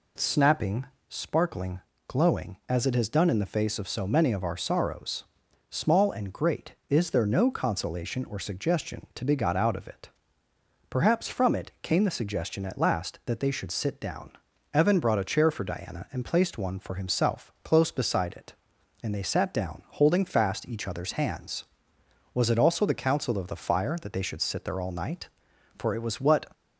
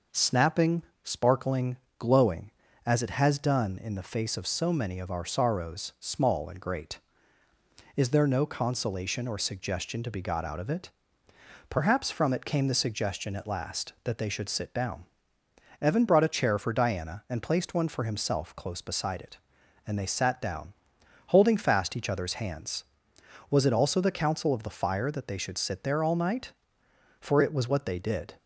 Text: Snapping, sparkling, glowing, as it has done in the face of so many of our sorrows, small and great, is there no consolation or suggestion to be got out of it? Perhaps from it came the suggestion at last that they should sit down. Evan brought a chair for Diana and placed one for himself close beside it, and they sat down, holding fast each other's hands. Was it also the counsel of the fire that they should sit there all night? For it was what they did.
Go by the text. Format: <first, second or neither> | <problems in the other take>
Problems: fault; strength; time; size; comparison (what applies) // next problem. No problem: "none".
second | stops before "they did"; at 26.5 s